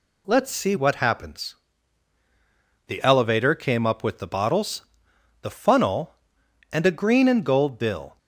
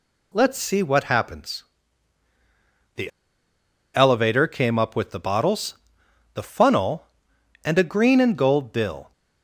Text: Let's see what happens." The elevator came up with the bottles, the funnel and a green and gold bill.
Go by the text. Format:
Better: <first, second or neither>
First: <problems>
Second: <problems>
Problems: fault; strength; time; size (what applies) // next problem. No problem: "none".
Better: first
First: none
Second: pauses between "The" and "elevator"; noticeable; at 3.1 s; 0.85 s long